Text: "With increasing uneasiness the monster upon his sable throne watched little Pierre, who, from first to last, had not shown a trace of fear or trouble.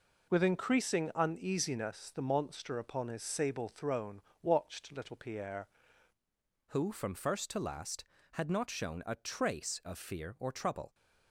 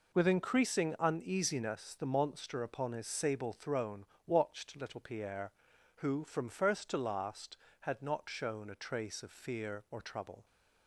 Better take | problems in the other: second | pauses between "throne" and "watched"; slight; at 4.1 s; 0.22 s long; slight in the second // changes voice at "who"; from 6.6 s on; 4.3 s long

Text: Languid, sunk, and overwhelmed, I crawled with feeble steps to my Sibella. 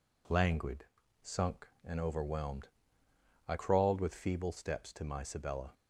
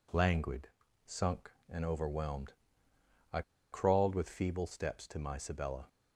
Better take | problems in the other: first | pauses between "I" and "crawled"; slight; at 3.4 s; 0.30 s long

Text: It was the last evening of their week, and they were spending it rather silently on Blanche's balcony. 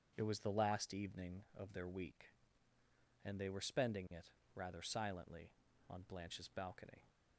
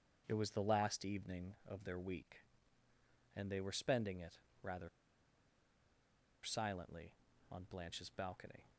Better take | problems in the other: first | starts louder than the rest; until 1.2 s; 7 dB; also in the first // pauses between "it" and "rather"; slight; at 4.3 s; 0.24 s long; slight in the first // pauses between "rather" and "silently"; strong; at 4.8 s; 1.5 s long

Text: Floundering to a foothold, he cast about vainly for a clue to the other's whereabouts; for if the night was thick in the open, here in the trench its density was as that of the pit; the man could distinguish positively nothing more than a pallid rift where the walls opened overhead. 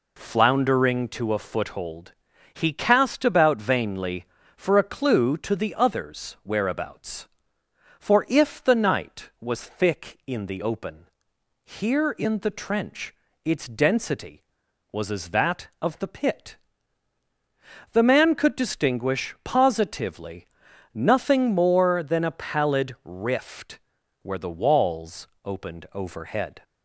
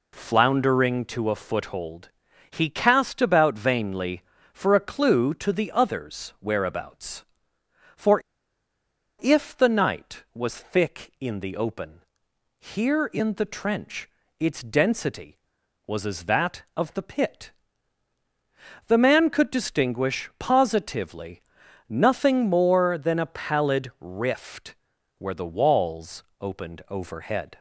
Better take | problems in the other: first | pauses between "for" and "if"; at 8.2 s; 0.99 s long // pauses between "trench" and "its"; slight; at 14.0 s; 0.30 s long; slight in the first // pauses between "positively" and "nothing"; noticeable; at 21.4 s; 0.48 s long; noticeable in the first // pauses between "rift" and "where"; at 24.7 s; 0.44 s long; also in the first // pauses between "walls" and "opened"; slight; at 26.2 s; 0.16 s long; slight in the first

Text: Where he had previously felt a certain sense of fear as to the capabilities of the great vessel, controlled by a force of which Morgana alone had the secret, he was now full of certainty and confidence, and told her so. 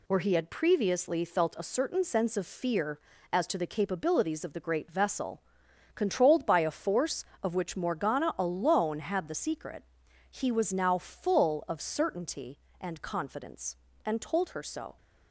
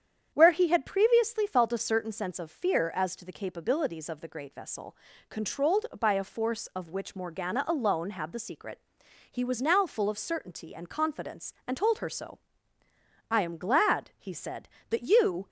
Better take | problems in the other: first | starts louder than the rest; strong; until 1.3 s; 8.5 dB // goes on to say "I am glad he said that you"; strong; from 13.3 s on; 2.1 s long

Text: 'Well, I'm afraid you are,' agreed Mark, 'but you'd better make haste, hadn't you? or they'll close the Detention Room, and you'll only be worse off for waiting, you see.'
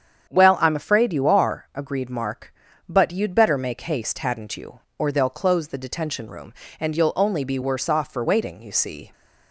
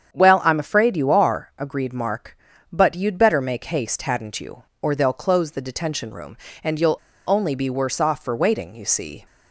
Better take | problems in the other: first | starts louder than the rest; strong; until 1.1 s; 8 dB; strong in the first // pauses between "you'll" and "only"; slight; at 6.9 s; 0.29 s long

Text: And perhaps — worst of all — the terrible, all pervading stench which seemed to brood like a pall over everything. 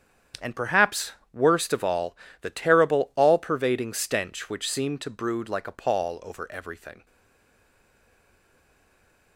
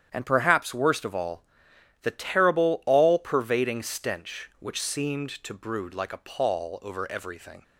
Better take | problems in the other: second | starts louder than the rest; strong; until 1.6 s; 8.5 dB; strong in the second // stays silent after the last word; from 7.0 s on; 2.3 s long

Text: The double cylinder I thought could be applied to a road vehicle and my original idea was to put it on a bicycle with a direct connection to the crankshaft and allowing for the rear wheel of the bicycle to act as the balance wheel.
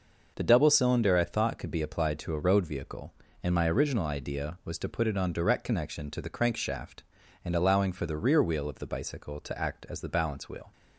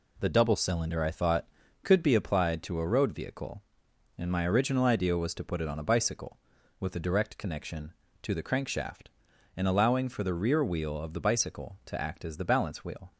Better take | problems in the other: second | skips "a bicycle with a"; at 5.3 s

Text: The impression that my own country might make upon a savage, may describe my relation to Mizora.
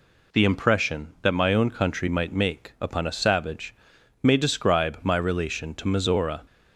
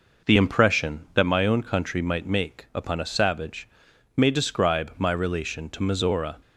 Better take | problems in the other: first | starts louder than the rest; noticeable; until 1.4 s; 5 dB

